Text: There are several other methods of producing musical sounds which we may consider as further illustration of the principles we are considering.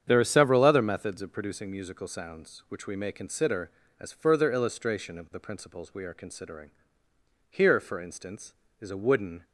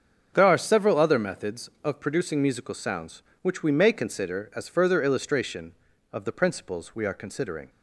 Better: second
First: starts louder than the rest; strong; until 1.0 s; 8 dB // goes on to say "Here for instance is a wooden"; strong; from 7.4 s on; 1.9 s long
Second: starts louder than the rest; until 1.3 s; 7 dB

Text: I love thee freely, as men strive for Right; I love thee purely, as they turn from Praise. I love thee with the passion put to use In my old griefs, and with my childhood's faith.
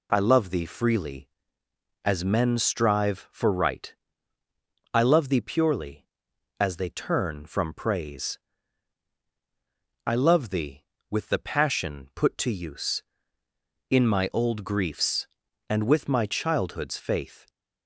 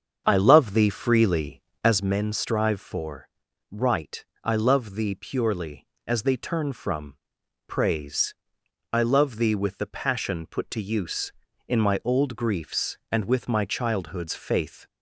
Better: first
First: none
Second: starts louder than the rest; strong; until 2.0 s; 7 dB // pauses between "for" and "Right"; at 3.2 s; 0.42 s long // pauses between "from" and "Praise"; noticeable; at 7.1 s; 0.50 s long

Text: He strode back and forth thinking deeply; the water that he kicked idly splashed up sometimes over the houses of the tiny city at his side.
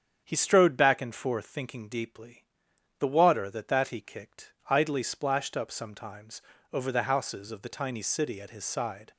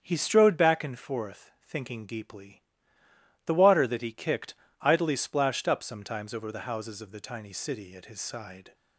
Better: second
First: starts louder than the rest; strong; until 1.2 s; 8 dB // says "that" twice; at 3.6 s // pauses between "kicked" and "idly"; slight; at 4.5 s; 0.18 s long // pauses between "sometimes" and "over"; slight; at 6.4 s; 0.32 s long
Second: starts louder than the rest; strong; until 1.0 s; 7.5 dB // pauses between "kicked" and "idly"; slight; at 4.5 s; 0.24 s long

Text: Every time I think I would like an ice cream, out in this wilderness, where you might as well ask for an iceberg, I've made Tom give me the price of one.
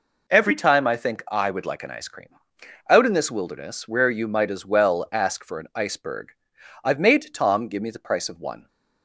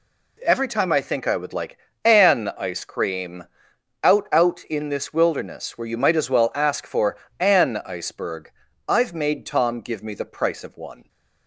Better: first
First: none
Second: pauses between "like" and "an"; slight; at 1.7 s; 0.26 s long // says "out" twice; at 4.3 s // pauses between "for" and "an"; slight; at 7.1 s; 0.24 s long

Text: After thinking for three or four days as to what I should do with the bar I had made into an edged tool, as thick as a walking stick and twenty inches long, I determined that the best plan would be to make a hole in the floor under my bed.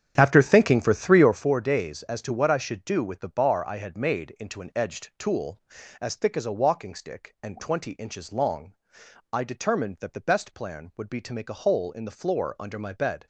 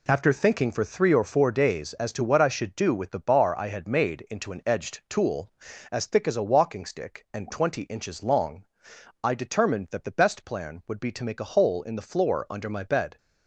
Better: second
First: starts louder than the rest; strong; until 1.4 s; 9 dB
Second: none

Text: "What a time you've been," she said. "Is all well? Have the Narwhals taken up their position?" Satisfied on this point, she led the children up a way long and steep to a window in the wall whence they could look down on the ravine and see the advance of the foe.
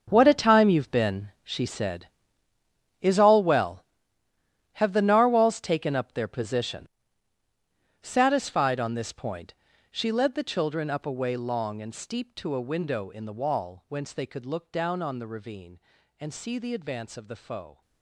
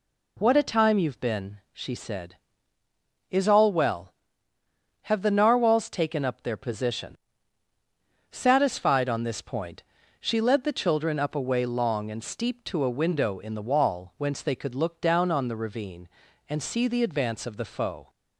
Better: second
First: gets quieter; strong; throughout; 15 dB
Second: none

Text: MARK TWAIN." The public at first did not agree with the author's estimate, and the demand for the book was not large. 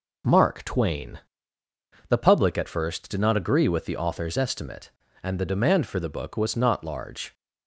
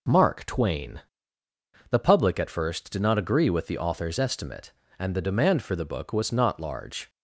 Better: neither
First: none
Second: none

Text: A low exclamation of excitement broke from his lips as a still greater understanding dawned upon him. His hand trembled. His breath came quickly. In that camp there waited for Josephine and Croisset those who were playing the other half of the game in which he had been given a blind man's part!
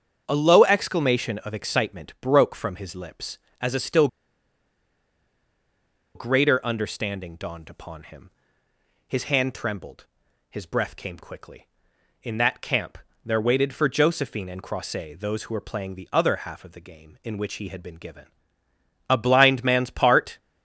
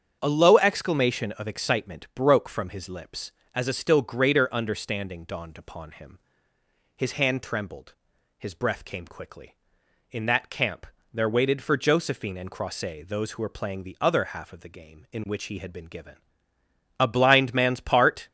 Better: second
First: starts louder than the rest; strong; until 1.2 s; 7.5 dB // pauses between "still" and "greater"; strong; at 4.0 s; 2.0 s long // pauses between "camp" and "there"; slight; at 12.9 s; 0.26 s long // pauses between "given" and "a"; noticeable; at 18.2 s; 0.82 s long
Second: starts louder than the rest; strong; until 1.2 s; 8 dB // pauses between "camp" and "there"; slight; at 10.8 s; 0.26 s long // pauses between "given" and "a"; noticeable; at 16.1 s; 0.82 s long

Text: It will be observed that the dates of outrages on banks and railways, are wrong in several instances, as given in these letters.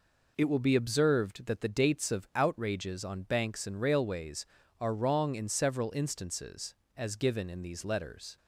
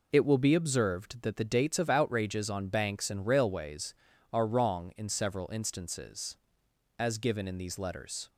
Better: neither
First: none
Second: none

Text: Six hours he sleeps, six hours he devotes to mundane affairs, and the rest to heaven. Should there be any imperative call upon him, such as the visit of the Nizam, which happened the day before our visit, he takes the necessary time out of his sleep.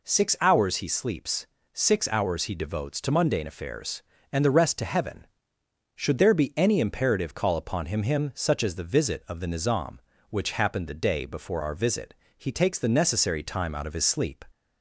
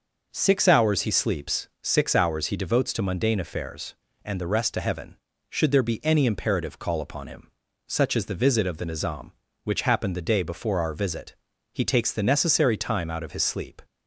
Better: second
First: says "him" twice; at 8.0 s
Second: none

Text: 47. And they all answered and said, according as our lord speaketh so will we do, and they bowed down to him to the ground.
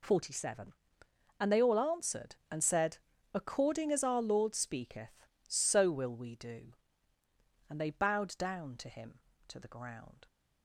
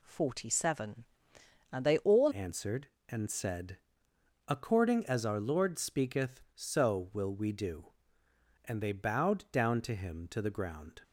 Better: first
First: none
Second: changes voice at "answered"; from 2.3 s on; 8.7 s long

